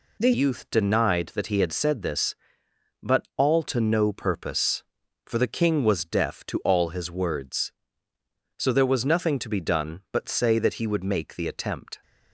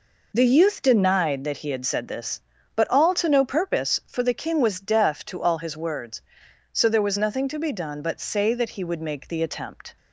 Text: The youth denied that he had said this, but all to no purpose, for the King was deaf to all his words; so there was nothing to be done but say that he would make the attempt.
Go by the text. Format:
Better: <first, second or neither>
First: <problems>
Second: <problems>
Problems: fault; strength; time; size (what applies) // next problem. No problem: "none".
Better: second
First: changes voice at "youth"; from 0.3 s on; 11.7 s long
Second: none